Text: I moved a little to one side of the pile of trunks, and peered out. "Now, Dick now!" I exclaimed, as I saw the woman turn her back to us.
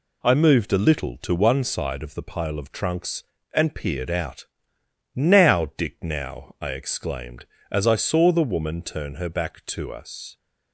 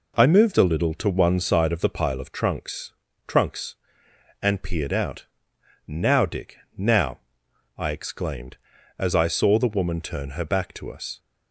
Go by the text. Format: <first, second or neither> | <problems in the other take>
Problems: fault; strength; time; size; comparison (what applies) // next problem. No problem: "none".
first | says "trunks" twice; at 3.2 s // pauses between "Dick" and "now"; slight; at 6.5 s; 0.20 s long